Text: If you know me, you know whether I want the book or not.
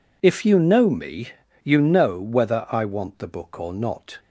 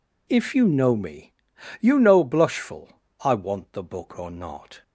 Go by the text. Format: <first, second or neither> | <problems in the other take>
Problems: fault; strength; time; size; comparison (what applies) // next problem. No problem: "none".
first | says "blushful" for "whether"; at 2.2 s